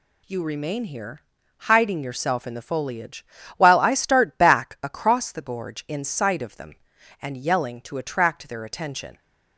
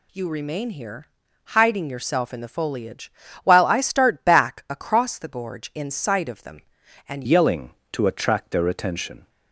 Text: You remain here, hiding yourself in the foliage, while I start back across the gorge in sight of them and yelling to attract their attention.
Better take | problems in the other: first | changes voice at "yelling"; from 7.2 s on; 2.0 s long

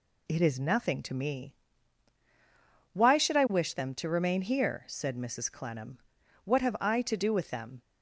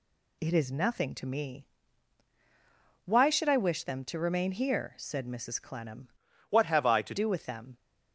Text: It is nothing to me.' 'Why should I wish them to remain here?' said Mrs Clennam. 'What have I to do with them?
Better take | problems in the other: first | changes voice from "What" to "to"; from 6.5 to 7.1 s; 0.6 s long

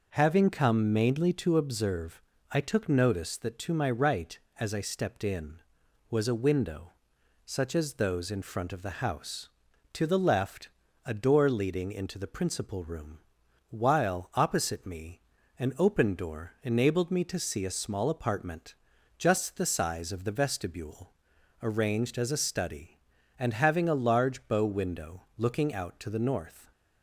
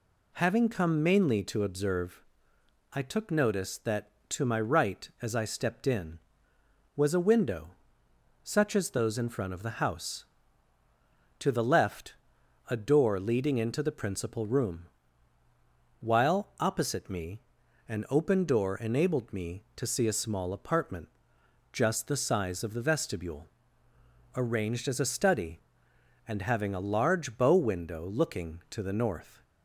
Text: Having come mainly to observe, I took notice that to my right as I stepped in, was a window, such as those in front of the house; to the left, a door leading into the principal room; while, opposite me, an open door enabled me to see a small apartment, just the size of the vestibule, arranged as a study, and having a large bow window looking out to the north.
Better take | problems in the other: first | skips "out"; at 28.6 s

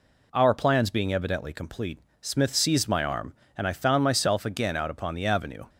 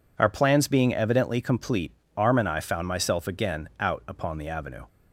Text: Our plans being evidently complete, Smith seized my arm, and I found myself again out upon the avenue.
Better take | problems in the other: first | skips "Smith seized my"; at 2.0 s

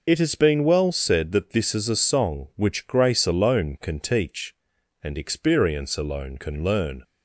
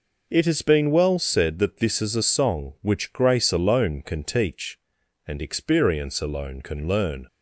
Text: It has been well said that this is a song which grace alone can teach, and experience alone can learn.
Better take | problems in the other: second | loses the start of "It"; at 0.0 s; 45 ms

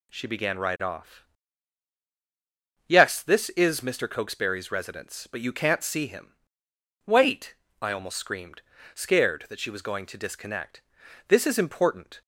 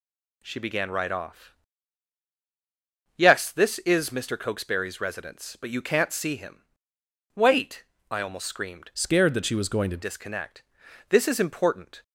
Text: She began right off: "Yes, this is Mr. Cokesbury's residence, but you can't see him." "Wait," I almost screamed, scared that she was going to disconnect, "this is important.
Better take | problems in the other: first | changes voice from "scared" to "to"; from 8.9 to 10.0 s; 1.1 s long

